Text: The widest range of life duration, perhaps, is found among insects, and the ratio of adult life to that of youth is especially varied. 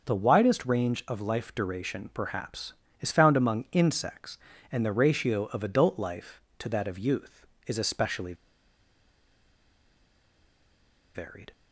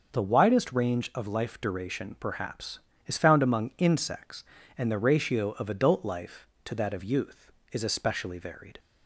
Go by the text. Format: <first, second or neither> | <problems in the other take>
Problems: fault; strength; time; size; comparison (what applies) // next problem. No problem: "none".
second | pauses between "especially" and "varied"; strong; at 8.3 s; 2.8 s long